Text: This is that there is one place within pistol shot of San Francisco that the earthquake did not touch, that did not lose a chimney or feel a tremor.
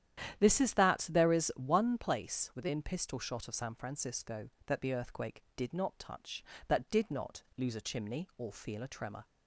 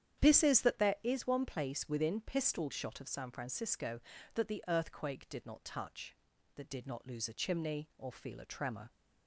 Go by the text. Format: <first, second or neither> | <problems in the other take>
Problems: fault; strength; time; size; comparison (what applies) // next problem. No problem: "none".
neither | starts louder than the rest; strong; the same in both